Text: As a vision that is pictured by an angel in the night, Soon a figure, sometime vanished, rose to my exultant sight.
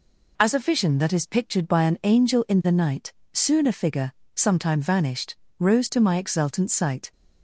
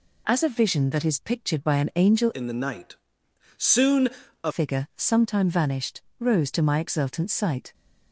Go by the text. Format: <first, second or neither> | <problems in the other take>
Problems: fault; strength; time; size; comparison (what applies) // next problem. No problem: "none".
first | changes voice from "in" to "a"; from 2.3 to 4.5 s; 2.2 s long // pauses between "Soon" and "a"; slight; at 4.0 s; 0.34 s long